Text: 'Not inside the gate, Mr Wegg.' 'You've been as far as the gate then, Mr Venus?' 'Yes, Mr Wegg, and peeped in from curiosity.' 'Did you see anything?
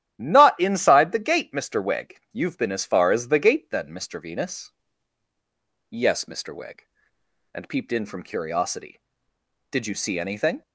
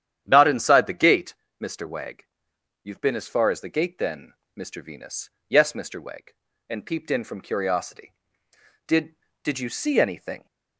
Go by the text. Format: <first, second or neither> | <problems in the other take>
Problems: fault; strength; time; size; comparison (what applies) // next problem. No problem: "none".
first | starts louder than the rest; strong; until 1.2 s; 10 dB; strong in the first // says "Did" twice; at 9.4 s